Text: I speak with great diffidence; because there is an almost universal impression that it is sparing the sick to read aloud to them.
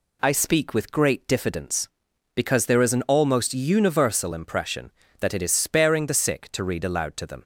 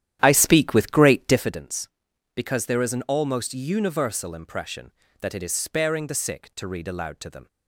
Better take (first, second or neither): first